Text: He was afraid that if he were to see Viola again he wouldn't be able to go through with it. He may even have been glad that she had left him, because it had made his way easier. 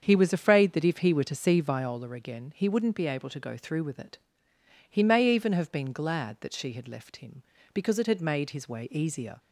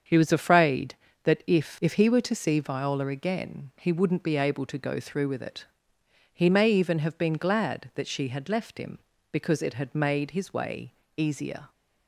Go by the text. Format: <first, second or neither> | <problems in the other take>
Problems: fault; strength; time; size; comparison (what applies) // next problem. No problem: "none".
first | starts louder than the rest; strong; until 1.3 s; 7 dB; strong in the first // says "if" twice; at 1.8 s // pauses between "way" and "easier"; slight; at 10.9 s; 0.24 s long